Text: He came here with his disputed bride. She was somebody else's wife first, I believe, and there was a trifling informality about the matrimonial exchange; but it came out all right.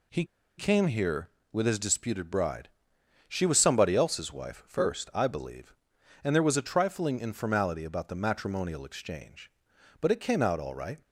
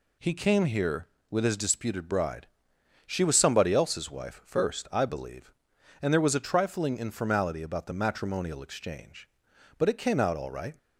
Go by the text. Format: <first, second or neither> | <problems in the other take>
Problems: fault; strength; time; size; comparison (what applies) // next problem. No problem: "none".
second | pauses between "He" and "came"; slight; at 0.2 s; 0.33 s long